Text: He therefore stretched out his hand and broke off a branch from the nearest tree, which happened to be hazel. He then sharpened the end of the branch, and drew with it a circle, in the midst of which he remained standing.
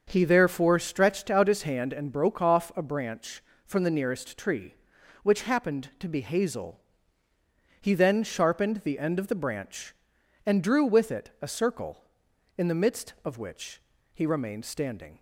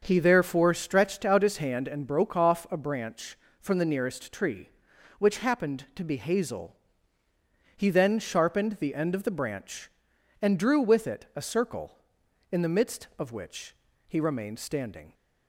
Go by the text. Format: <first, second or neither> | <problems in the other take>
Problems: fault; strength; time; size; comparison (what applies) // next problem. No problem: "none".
neither | starts louder than the rest; the same in both // pauses between "which" and "he"; slight; the same in both